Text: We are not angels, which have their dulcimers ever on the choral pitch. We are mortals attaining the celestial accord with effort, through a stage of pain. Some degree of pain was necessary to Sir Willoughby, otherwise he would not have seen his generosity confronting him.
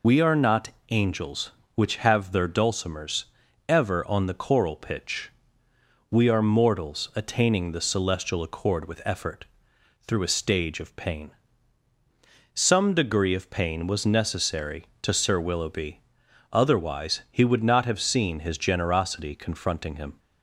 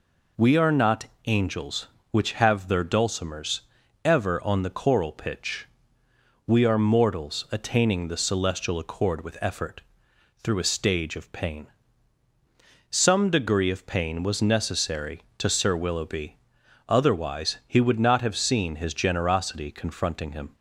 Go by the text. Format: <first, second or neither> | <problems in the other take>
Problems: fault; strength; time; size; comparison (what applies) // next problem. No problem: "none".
second | loses the start of "We"; at 0.0 s; 40 ms // pauses between "not" and "angels"; slight; at 0.6 s; 0.22 s long; slight in the second // pauses between "dulcimers" and "ever"; at 3.2 s; 0.42 s long; also in the second